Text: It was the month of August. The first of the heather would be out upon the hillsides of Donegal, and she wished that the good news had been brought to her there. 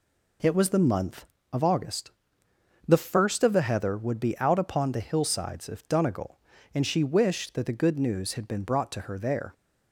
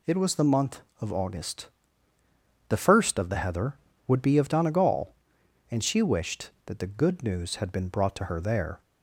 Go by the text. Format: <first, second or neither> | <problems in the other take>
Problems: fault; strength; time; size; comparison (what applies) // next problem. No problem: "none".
first | skips "out upon the hillsides"; at 4.3 s